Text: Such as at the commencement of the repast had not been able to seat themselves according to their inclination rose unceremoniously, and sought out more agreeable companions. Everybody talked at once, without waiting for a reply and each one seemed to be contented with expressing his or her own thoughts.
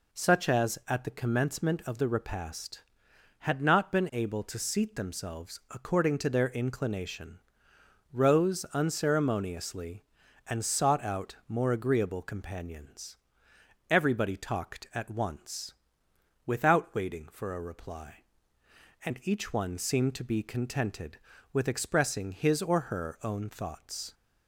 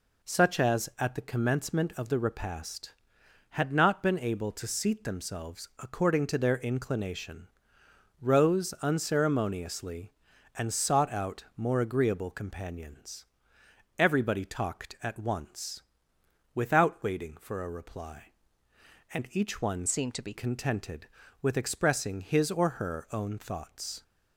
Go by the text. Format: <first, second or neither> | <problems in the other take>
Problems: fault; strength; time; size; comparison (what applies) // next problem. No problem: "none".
first | pauses between "inclination" and "rose"; noticeable; at 7.4 s; 0.74 s long; noticeable in the first // changes voice from "seemed" to "be"; from 19.8 to 20.3 s; 0.5 s long